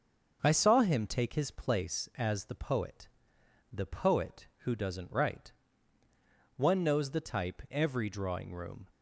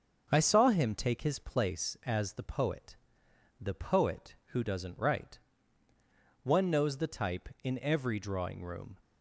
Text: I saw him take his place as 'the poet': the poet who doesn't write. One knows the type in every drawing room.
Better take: second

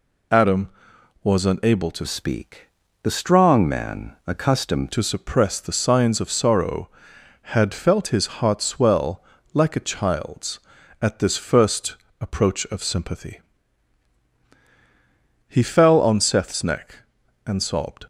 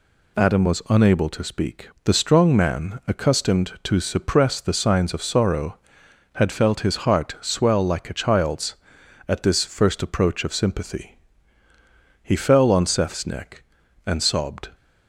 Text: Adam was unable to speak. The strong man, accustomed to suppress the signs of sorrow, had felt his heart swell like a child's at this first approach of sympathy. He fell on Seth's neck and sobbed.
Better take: second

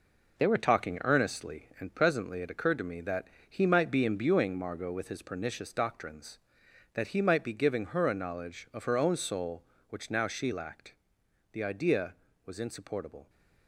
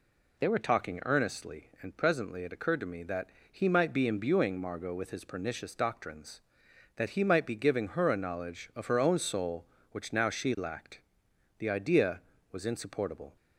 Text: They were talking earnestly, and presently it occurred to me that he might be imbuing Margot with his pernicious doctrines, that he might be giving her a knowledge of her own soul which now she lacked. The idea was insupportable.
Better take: second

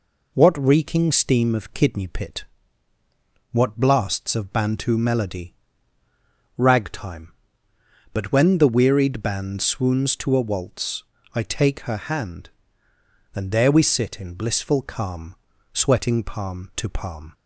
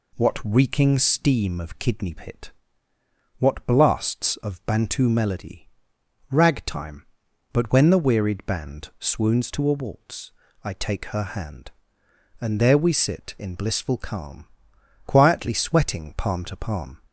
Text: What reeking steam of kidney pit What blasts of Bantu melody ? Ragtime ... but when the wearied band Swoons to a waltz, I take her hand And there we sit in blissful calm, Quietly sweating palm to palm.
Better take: second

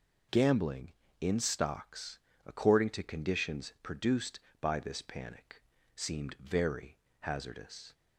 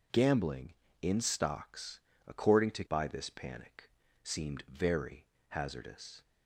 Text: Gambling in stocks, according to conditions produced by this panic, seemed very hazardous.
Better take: first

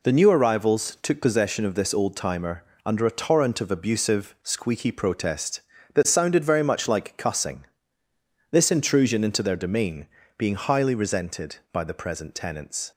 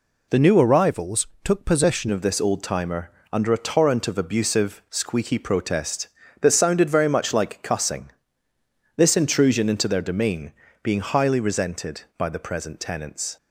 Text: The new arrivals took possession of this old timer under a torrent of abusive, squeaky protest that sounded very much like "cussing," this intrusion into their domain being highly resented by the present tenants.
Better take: first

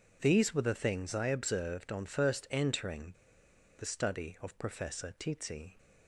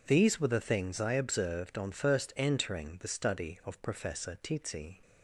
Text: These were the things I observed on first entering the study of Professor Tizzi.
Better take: second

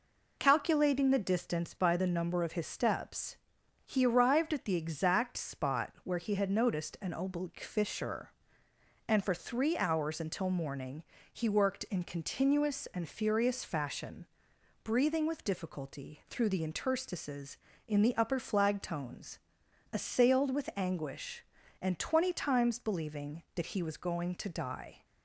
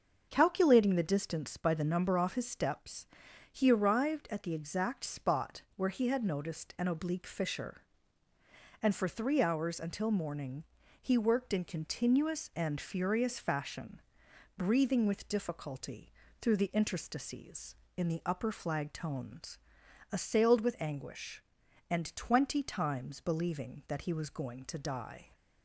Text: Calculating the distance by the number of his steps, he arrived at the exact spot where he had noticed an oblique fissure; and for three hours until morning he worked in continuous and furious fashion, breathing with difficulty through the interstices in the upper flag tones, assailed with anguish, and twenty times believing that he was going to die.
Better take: first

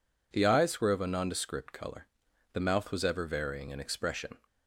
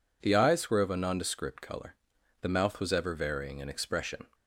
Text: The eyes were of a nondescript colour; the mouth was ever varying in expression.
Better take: neither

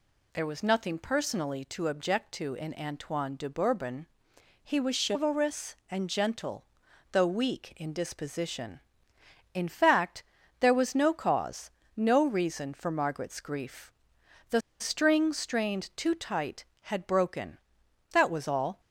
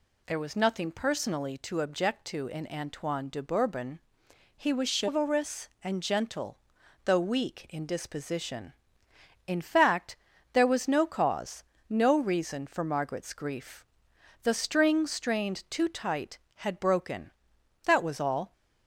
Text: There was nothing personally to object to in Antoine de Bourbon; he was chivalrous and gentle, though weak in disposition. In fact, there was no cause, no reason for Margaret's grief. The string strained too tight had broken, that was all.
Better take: second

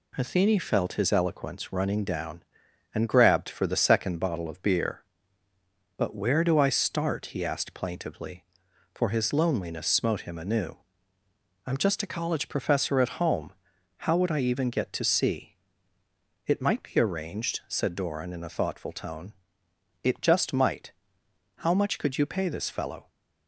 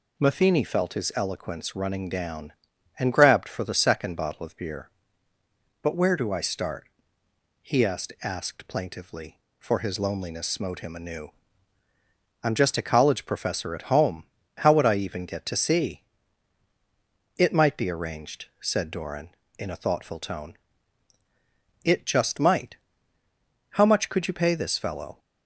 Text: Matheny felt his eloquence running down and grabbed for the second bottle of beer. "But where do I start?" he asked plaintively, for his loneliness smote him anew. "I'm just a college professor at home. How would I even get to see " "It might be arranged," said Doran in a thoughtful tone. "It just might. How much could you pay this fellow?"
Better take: first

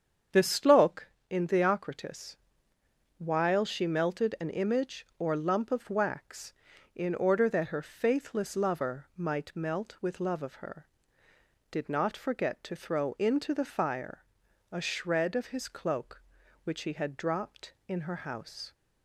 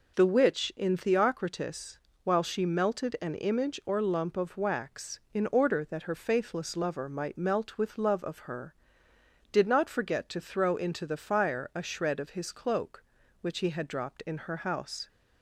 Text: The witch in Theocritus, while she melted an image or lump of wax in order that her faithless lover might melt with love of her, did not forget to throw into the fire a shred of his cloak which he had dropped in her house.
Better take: second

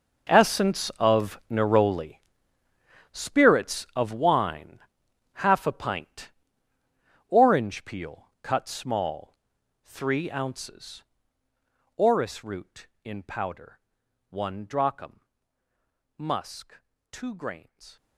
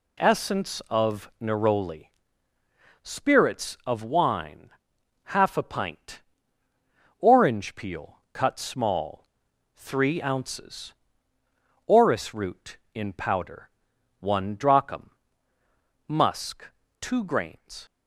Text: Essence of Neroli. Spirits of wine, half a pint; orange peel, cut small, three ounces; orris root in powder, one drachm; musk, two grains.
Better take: second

